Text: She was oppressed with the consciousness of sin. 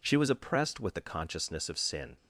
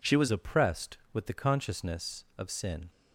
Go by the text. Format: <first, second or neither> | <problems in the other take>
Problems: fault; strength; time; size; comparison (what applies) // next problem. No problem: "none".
first | changes voice at "oppressed"; from 0.3 s on; 2.6 s long